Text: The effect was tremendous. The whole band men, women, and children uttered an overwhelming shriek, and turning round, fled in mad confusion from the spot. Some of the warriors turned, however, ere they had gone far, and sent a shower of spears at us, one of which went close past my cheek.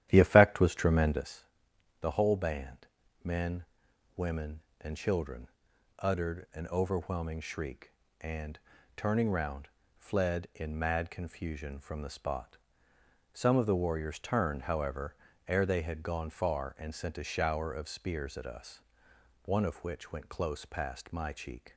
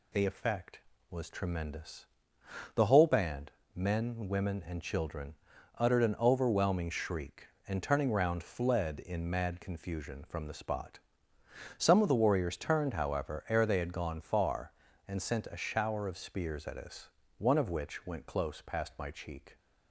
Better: second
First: starts louder than the rest; strong; until 1.3 s; 11.5 dB // pauses between "band" and "men"; at 2.8 s; 0.38 s long // pauses between "children" and "uttered"; noticeable; at 5.4 s; 0.50 s long // pauses between "and" and "turning"; at 8.5 s; 0.38 s long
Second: pauses between "band" and "men"; slight; at 3.4 s; 0.26 s long // pauses between "children" and "uttered"; noticeable; at 5.3 s; 0.46 s long

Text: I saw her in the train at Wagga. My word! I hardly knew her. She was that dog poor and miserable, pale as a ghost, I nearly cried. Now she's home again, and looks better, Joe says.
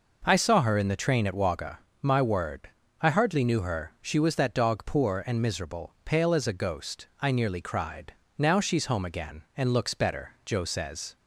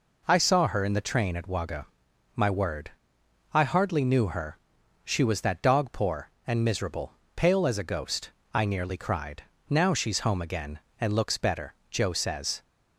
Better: neither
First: none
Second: none

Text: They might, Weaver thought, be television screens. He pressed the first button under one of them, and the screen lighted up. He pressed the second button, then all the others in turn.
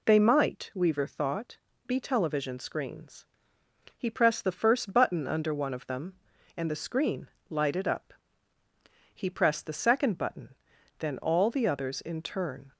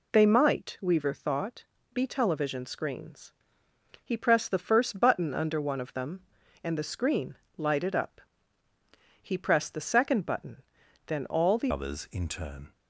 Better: first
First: pauses between "screen" and "lighted"; slight; at 7.2 s; 0.22 s long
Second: pauses between "screen" and "lighted"; slight; at 7.3 s; 0.22 s long // changes voice at "others"; from 11.7 s on; 1.0 s long

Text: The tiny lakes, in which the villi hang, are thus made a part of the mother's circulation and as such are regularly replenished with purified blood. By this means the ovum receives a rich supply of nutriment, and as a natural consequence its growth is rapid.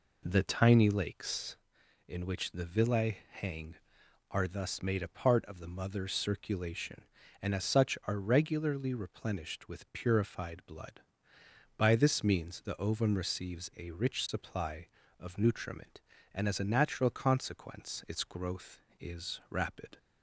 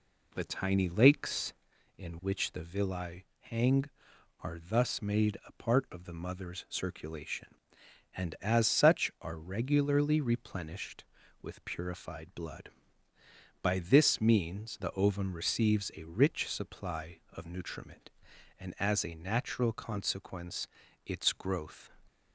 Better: first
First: none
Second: pauses between "villi" and "hang"; slight; at 3.2 s; 0.16 s long // pauses between "consequence" and "its"; slight; at 20.6 s; 0.36 s long // stops before "is rapid"; at 22.0 s

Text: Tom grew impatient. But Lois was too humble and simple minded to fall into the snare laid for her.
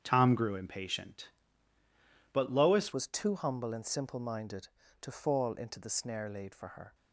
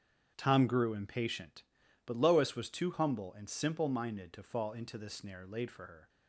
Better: second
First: starts louder than the rest; strong; until 1.0 s; 8.5 dB // changes voice at "was"; from 2.9 s on; 4.0 s long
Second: starts louder than the rest; strong; until 1.3 s; 8 dB

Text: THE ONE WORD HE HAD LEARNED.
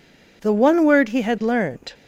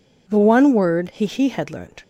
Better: first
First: none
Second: says "HE" twice; at 1.2 s

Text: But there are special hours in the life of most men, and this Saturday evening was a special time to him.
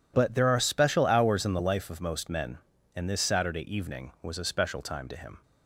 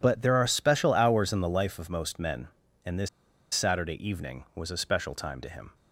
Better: first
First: none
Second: pauses between "this" and "Saturday"; at 3.0 s; 0.45 s long

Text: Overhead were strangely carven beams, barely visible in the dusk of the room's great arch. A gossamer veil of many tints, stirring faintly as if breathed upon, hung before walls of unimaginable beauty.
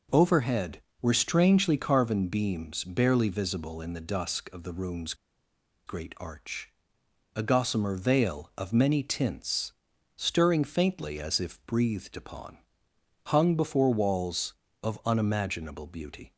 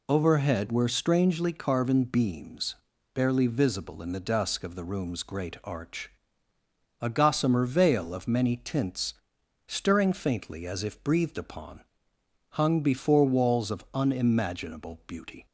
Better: second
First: pauses between "room's" and "great"; noticeable; at 5.1 s; 0.73 s long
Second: none

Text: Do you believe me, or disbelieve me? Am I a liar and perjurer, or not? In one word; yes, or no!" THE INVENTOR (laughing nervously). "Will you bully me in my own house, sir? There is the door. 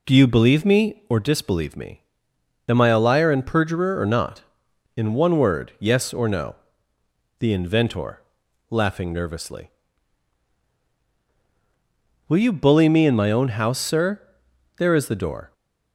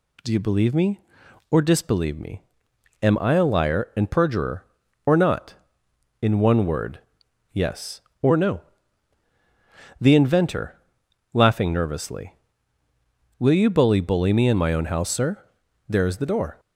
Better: first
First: none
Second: says "bully" twice; at 14.0 s

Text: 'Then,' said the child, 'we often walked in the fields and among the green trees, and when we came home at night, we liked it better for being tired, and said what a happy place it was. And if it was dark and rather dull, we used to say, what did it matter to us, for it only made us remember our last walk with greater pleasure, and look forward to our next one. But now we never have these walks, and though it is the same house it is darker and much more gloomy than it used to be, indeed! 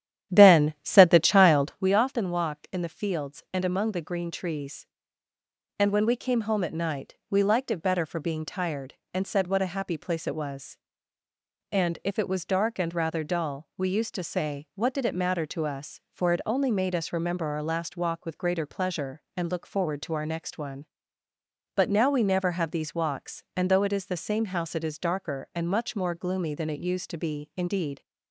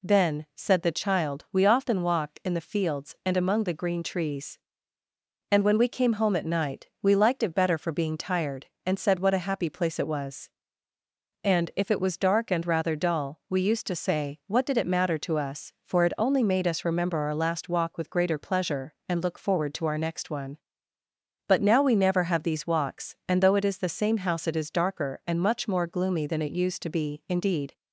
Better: second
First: starts louder than the rest; strong; until 1.8 s; 11 dB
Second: none

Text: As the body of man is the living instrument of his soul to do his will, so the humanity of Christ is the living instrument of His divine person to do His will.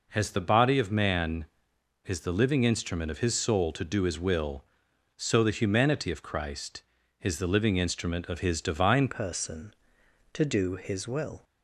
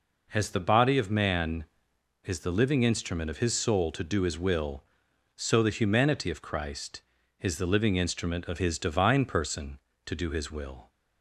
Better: second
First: changes voice at "person"; from 9.0 s on; 2.4 s long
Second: none

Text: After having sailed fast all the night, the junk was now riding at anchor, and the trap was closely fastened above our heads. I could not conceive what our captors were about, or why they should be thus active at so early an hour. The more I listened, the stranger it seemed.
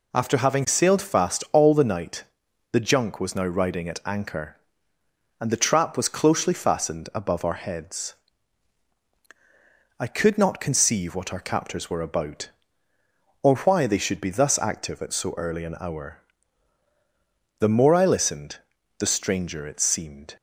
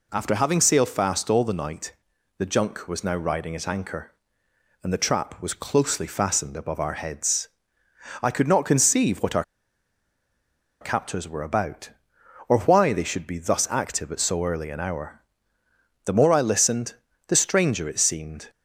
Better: first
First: none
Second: pauses between "our" and "captors"; strong; at 9.4 s; 1.3 s long

